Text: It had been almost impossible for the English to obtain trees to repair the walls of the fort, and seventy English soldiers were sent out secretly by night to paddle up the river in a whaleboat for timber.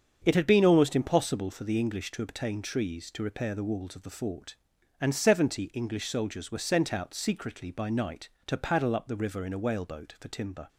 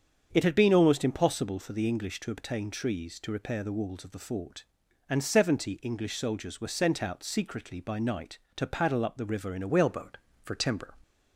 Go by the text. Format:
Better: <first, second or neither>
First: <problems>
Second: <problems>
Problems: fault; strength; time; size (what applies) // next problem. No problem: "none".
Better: first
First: starts louder than the rest; until 1.2 s; 7 dB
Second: starts louder than the rest; strong; until 1.3 s; 7 dB // changes voice at "whaleboat"; from 9.6 s on; 1.3 s long